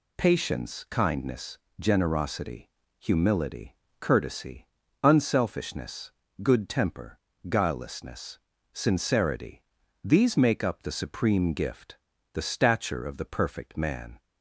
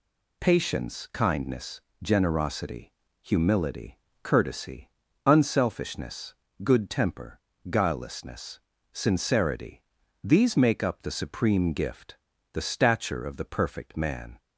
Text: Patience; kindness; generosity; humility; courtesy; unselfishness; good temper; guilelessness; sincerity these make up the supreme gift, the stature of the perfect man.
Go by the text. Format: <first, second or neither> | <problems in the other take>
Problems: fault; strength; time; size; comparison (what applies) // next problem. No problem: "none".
neither | pauses between "sincerity" and "these"; the same in both